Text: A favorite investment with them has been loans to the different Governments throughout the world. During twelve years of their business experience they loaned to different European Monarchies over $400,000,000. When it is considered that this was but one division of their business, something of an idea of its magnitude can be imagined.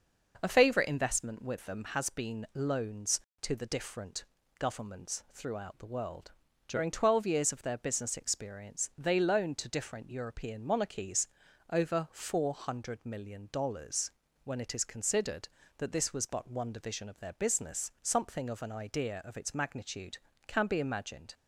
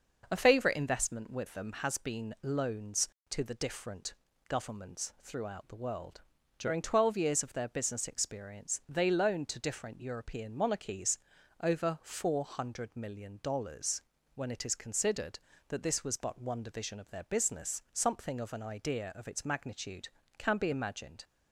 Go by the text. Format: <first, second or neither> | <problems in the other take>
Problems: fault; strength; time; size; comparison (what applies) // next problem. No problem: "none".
neither | pauses between "different" and "Governments"; slight; the same in both // pauses between "Monarchies" and "over"; the same in both